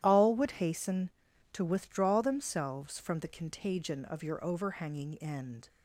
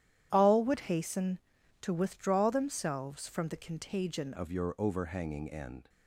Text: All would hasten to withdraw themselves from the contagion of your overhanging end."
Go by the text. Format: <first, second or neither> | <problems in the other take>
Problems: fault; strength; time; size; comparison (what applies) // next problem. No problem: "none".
first | starts louder than the rest; strong; until 1.3 s; 11.5 dB; strong in the first // changes voice at "of"; from 4.3 s on; 1.5 s long